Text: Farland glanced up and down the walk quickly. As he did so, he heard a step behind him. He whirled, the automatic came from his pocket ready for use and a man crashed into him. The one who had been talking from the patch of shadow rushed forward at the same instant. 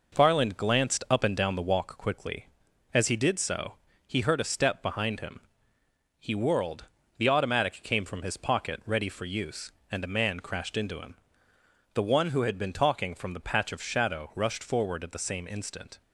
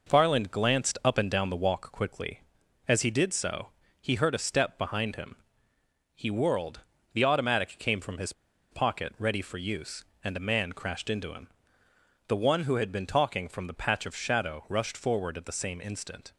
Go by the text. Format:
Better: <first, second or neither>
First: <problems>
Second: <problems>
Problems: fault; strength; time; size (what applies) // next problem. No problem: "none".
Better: first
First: none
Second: pauses between "his" and "pocket"; at 8.3 s; 0.39 s long